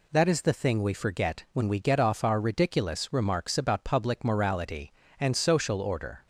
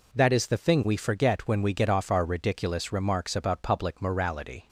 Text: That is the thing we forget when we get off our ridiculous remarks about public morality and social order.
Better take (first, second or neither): first